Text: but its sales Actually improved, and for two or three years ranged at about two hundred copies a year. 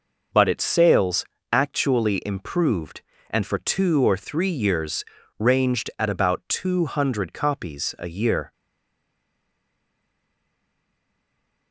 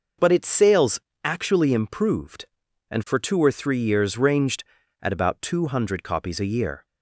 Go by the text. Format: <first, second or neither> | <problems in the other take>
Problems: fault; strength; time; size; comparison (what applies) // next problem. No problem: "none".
second | pauses between "sales" and "Actually"; slight; at 1.2 s; 0.26 s long; slight in the second // pauses between "years" and "ranged"; slight; at 5.0 s; 0.36 s long // stays silent after the last word; strong; from 8.5 s on; 3.2 s long